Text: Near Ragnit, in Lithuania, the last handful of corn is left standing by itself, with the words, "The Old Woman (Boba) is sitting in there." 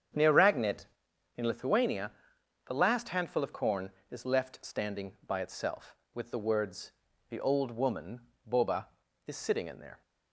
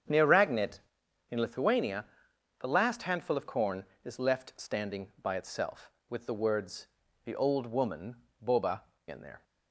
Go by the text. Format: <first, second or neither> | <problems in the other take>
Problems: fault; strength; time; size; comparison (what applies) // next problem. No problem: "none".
first | starts louder than the rest; strong; until 1.6 s; 8 dB; strong in the first // skips "is sitting"; at 8.9 s